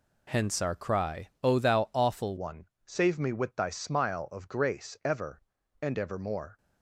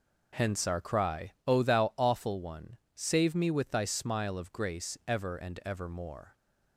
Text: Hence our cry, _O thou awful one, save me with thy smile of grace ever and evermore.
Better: second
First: changes voice at "one"; from 2.3 s on; 4.2 s long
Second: none

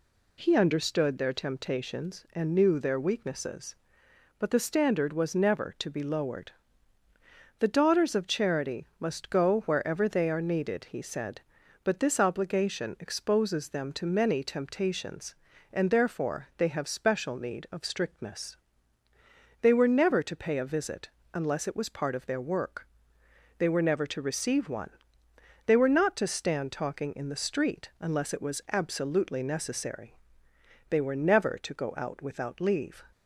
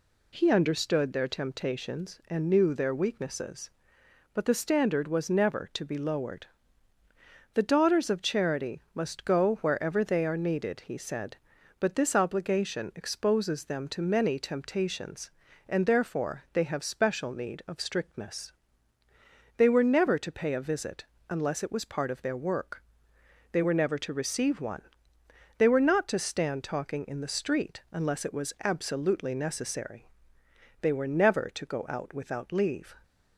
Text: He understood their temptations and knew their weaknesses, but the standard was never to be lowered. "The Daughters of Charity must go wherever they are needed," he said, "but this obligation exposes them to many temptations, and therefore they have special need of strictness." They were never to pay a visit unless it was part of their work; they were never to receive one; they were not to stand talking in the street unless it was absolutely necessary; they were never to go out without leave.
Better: neither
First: pauses between "visit" and "unless"; slight; at 21.0 s; 0.26 s long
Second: pauses between "visit" and "unless"; slight; at 21.0 s; 0.26 s long

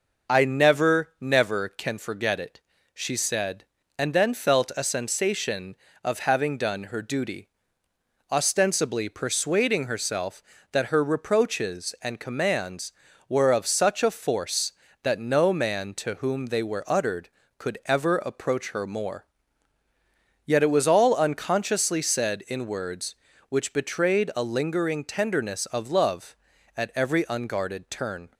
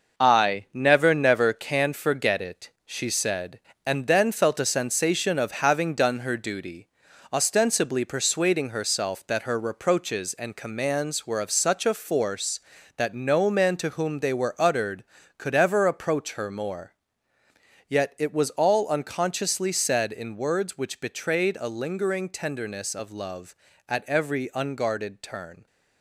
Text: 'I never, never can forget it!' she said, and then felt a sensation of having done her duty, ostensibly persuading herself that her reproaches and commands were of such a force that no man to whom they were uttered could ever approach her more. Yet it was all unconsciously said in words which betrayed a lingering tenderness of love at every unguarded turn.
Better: first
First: none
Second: gets quieter; throughout; 6.5 dB

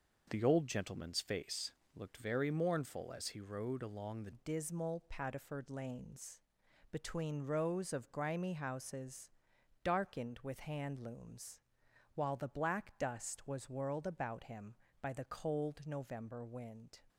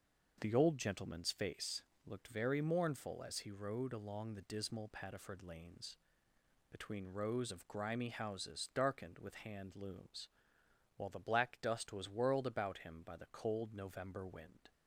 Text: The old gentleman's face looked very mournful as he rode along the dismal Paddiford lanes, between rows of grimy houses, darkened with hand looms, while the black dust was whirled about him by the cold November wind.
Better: second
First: pauses between "face" and "looked"; slight; at 1.7 s; 0.24 s long // changes voice at "dismal"; from 4.3 s on; 12.7 s long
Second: pauses between "face" and "looked"; slight; at 1.8 s; 0.24 s long

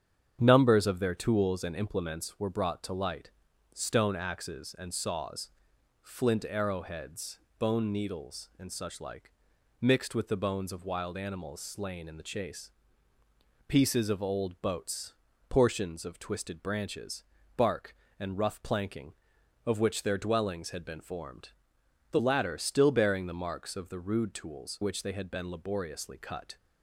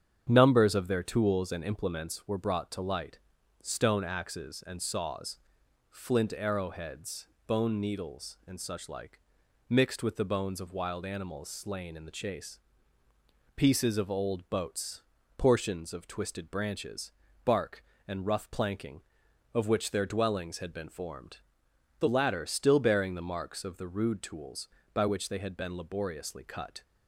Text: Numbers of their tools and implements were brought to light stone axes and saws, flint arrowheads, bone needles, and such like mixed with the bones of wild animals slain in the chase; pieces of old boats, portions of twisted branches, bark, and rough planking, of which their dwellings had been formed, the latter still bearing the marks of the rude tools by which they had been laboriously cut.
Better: second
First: starts louder than the rest; strong; until 1.4 s; 8.5 dB // pauses between "light" and "stone"; at 3.2 s; 0.44 s long // pauses between "like" and "mixed"; noticeable; at 9.3 s; 0.50 s long // skips "by"; at 24.8 s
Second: starts louder than the rest; strong; until 1.3 s; 8.5 dB // pauses between "light" and "stone"; at 3.1 s; 0.44 s long // pauses between "like" and "mixed"; noticeable; at 9.1 s; 0.50 s long

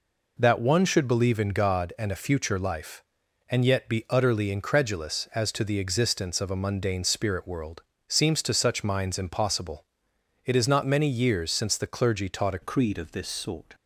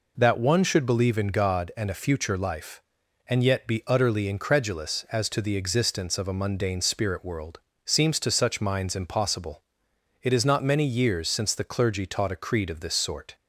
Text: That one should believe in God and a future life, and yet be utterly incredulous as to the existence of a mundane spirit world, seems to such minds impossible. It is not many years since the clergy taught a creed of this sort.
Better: second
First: changes voice at "creed"; from 12.6 s on; 1.1 s long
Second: none

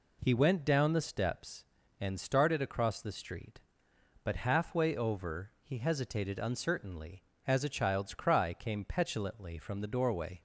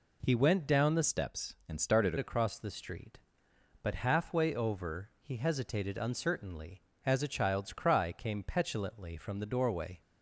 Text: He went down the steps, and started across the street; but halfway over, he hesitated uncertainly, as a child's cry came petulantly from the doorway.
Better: first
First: none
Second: changes voice from "steps" to "started"; from 1.0 to 2.1 s; 1.1 s long

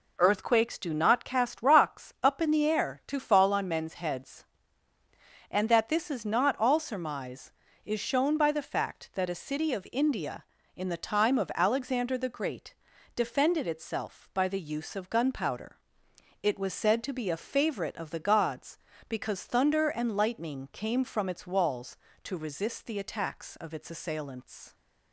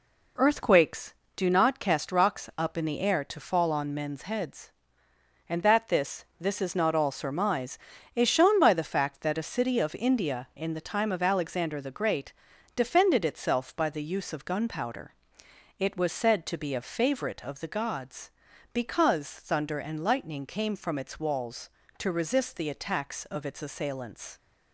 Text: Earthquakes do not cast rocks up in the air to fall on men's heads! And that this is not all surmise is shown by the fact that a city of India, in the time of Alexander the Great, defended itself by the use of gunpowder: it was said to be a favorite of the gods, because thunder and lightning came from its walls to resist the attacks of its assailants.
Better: first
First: none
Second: says "this" twice; at 6.3 s

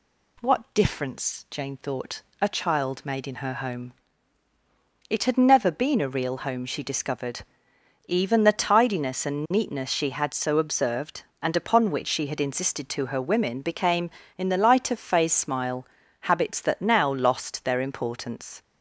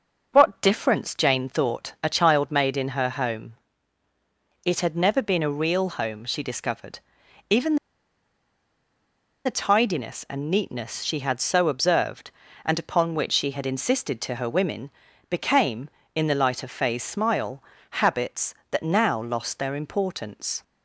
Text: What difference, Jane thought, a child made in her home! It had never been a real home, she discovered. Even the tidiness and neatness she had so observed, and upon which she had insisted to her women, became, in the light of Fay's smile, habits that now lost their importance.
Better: first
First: none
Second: starts louder than the rest; noticeable; until 1.3 s; 6 dB // pauses between "Even" and "the"; strong; at 7.7 s; 1.6 s long

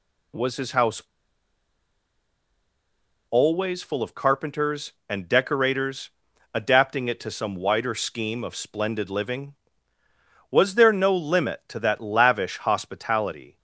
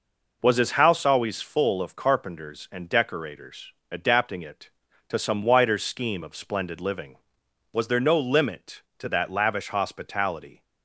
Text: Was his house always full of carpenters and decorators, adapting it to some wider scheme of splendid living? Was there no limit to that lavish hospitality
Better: second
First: pauses between "house" and "always"; strong; at 1.0 s; 2.3 s long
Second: none

